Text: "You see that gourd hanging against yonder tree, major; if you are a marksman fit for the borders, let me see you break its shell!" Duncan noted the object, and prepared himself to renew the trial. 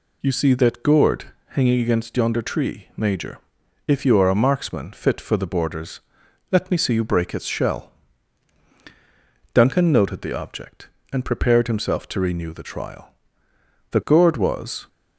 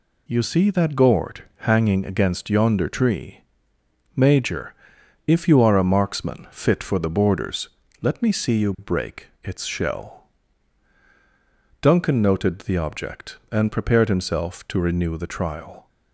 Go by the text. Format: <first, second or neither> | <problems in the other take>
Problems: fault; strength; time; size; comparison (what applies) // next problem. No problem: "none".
second | pauses between "gourd" and "hanging"; slight; at 1.2 s; 0.22 s long // goes on to say "The gourd was"; noticeable; from 13.9 s on; 0.97 s long